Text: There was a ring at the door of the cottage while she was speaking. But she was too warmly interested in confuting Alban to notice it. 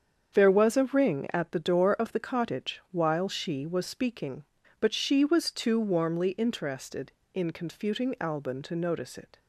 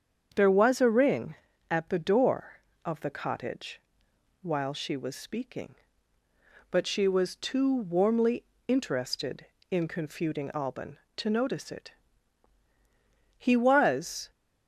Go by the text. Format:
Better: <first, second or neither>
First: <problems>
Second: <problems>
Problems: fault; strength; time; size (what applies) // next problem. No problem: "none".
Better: first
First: starts louder than the rest; strong; until 1.4 s; 7.5 dB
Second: starts louder than the rest; strong; until 1.3 s; 7.5 dB // pauses between "cottage" and "while"; noticeable; at 3.8 s; 0.60 s long // pauses between "warmly" and "interested"; slight; at 8.4 s; 0.22 s long // goes on to say "He was"; noticeable; from 13.3 s on; 0.94 s long